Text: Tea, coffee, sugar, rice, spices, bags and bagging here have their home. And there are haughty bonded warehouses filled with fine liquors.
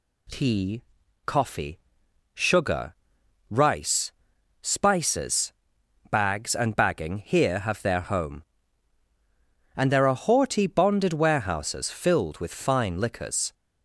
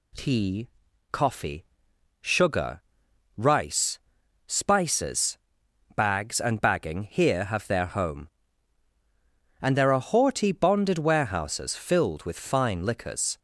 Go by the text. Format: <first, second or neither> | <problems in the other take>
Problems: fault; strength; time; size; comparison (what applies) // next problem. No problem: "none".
neither | none